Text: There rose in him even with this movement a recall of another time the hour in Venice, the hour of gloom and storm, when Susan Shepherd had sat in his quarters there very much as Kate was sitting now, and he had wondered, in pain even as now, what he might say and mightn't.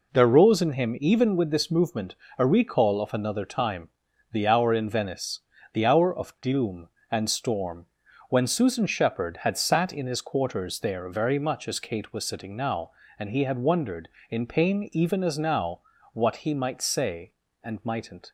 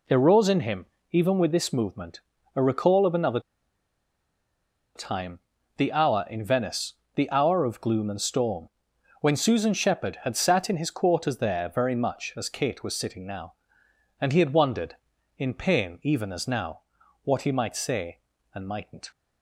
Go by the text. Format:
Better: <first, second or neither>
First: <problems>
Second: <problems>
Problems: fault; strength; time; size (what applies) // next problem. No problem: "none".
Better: first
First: pauses between "movement" and "a"; slight; at 2.1 s; 0.22 s long // pauses between "time" and "the"; at 3.8 s; 0.42 s long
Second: pauses between "him" and "even"; slight; at 0.8 s; 0.26 s long // pauses between "movement" and "a"; slight; at 2.1 s; 0.36 s long // pauses between "another" and "time"; strong; at 3.3 s; 1.5 s long // pauses between "time" and "the"; at 5.3 s; 0.38 s long